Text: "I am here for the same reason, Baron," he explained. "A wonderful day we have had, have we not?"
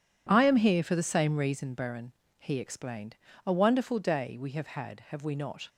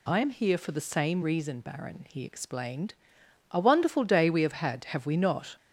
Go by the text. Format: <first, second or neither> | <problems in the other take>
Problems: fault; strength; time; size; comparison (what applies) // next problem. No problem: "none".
neither | none